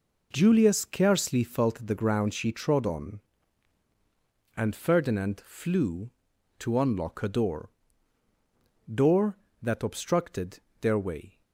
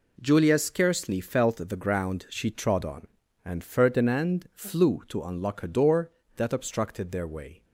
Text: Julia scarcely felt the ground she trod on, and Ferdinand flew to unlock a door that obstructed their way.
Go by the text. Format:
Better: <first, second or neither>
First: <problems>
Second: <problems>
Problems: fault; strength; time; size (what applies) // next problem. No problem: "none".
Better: second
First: says "door" twice; at 8.9 s // pauses between "obstructed" and "their"; slight; at 10.5 s; 0.20 s long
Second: none